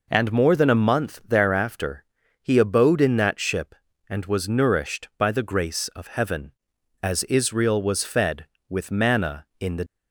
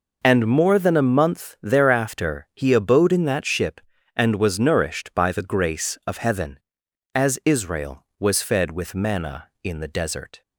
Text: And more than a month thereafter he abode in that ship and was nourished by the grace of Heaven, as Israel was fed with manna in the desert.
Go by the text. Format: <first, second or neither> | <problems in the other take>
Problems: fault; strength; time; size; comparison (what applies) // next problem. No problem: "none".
second | pauses between "thereafter" and "he"; at 2.0 s; 0.38 s long // stops before "desert"; at 9.8 s